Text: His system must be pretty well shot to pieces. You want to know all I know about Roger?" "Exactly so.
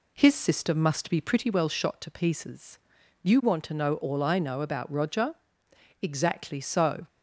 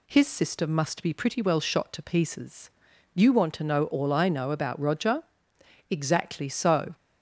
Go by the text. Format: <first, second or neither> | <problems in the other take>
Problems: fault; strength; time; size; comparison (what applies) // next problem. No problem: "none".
second | starts louder than the rest; slight; until 1.6 s; 2 dB